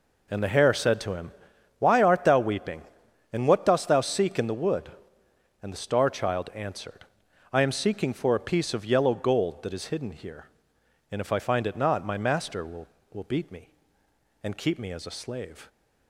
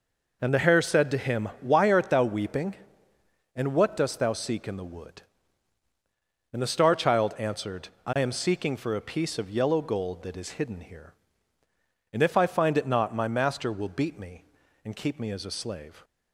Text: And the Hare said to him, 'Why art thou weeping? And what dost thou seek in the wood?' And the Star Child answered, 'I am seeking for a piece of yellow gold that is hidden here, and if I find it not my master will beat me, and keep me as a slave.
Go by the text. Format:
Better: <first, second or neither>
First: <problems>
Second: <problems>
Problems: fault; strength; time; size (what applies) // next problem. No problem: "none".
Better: second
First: says "will" twice; at 13.1 s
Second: none